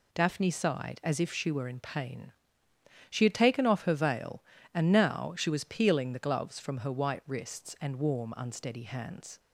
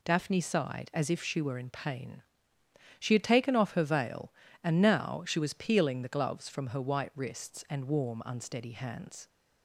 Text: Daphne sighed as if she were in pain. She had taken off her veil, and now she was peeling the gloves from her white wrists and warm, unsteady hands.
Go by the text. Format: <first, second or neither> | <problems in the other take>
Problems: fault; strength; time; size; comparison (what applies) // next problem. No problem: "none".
neither | none